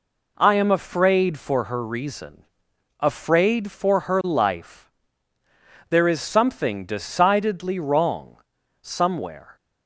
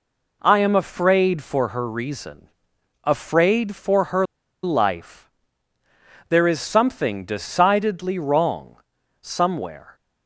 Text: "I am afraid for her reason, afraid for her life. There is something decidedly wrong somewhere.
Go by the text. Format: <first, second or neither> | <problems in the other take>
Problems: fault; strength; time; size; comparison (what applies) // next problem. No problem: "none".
first | pauses between "her" and "life"; at 4.2 s; 0.38 s long // pauses between "wrong" and "somewhere"; noticeable; at 8.7 s; 0.46 s long; noticeable in the first